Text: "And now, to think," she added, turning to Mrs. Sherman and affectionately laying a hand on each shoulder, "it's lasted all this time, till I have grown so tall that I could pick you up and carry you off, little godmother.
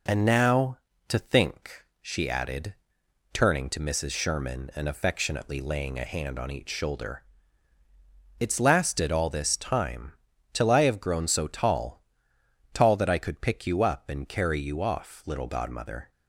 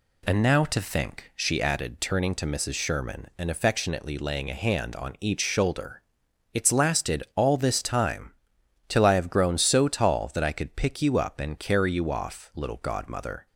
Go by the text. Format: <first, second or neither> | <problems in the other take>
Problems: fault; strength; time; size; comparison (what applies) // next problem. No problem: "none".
second | says "tall" twice; at 12.7 s